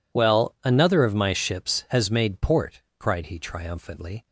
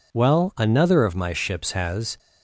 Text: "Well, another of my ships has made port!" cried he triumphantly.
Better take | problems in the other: first | stops before "made port cried he triumphantly"; at 2.1 s

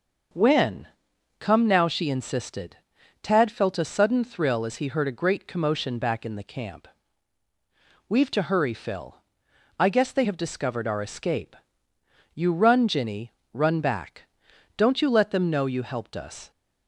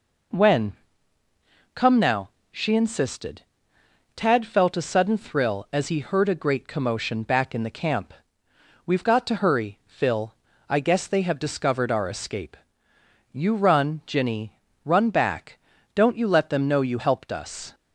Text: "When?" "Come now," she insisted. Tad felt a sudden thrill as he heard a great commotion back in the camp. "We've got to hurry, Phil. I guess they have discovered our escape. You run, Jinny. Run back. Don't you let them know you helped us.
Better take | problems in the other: second | starts louder than the rest; noticeable; until 1.8 s; 6 dB // skips "got"; at 8.3 s

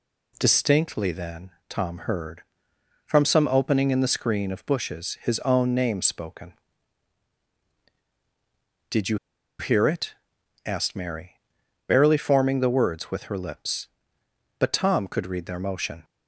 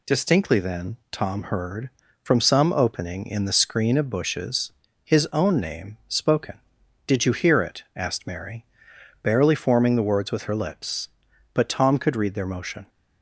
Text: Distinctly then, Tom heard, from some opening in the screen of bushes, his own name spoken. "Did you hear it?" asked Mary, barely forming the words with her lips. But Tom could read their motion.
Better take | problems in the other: second | pauses between "you" and "hear"; at 9.1 s; 0.42 s long

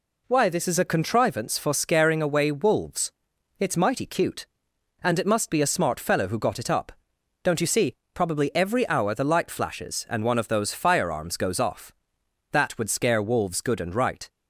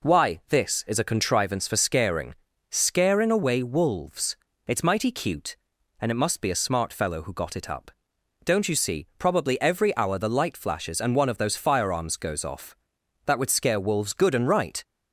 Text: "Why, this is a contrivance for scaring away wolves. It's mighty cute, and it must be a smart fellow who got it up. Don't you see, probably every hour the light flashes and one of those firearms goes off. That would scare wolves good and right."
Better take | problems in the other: first | says "scaring" twice; at 2.6 s

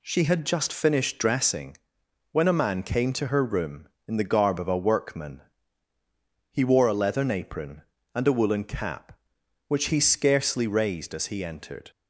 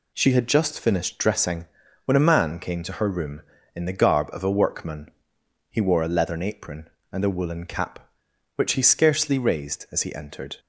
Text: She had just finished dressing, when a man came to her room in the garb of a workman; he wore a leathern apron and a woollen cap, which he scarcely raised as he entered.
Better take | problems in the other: neither | none

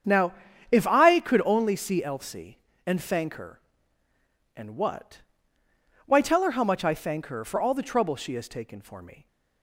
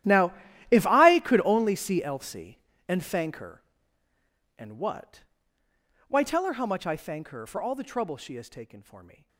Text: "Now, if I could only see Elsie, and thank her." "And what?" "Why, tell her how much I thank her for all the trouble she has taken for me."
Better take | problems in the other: first | gets quieter; strong; throughout; 19.5 dB // starts louder than the rest; strong; until 1.4 s; 13 dB; strong in the first

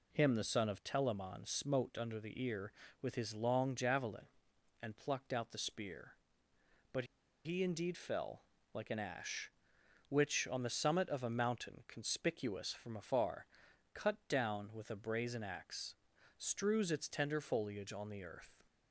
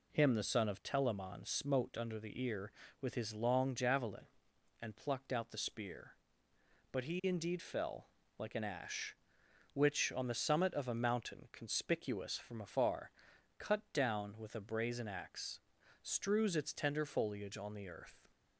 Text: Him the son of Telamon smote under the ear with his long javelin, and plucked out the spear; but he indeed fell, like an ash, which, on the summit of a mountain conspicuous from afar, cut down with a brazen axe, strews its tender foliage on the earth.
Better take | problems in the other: second | pauses between "but" and "he"; at 7.0 s; 0.39 s long

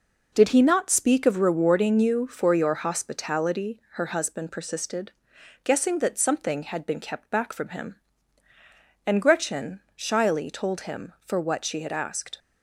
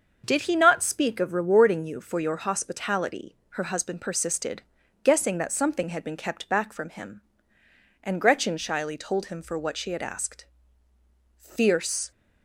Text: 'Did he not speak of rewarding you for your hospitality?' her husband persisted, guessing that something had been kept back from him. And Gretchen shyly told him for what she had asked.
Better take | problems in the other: first | starts louder than the rest; until 1.2 s; 6.5 dB // goes on to say "Fierce"; noticeable; from 11.3 s on; 0.74 s long

